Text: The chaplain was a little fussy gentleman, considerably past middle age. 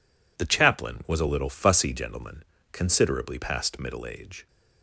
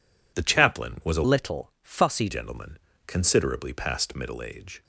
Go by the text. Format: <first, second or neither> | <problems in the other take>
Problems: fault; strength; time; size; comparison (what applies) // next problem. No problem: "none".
first | changes voice from "little" to "fussy"; from 1.2 to 2.2 s; 1.0 s long